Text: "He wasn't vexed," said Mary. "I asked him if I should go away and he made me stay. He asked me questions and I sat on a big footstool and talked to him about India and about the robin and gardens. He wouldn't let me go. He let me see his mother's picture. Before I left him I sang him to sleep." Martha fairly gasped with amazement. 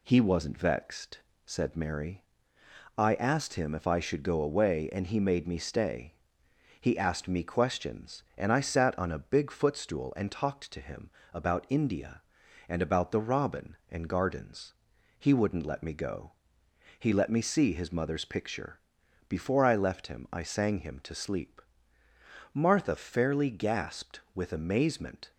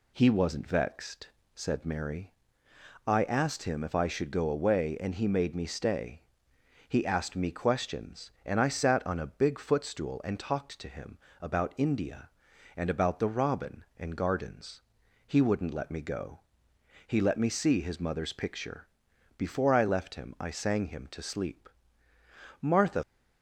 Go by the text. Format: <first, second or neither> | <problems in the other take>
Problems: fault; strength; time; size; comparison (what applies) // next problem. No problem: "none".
first | pauses between "him" and "about"; slight; at 11.1 s; 0.24 s long; slight in the first // stops before "fairly gasped with amazement"; at 23.0 s